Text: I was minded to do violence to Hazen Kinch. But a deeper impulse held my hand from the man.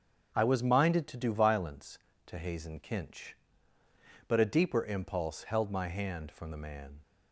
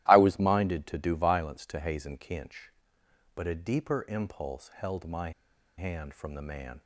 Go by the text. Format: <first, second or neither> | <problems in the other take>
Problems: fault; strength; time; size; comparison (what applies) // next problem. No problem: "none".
first | starts louder than the rest; strong; until 1.0 s; 14.5 dB; also in the first // pauses between "my" and "hand"; noticeable; at 5.3 s; 0.47 s long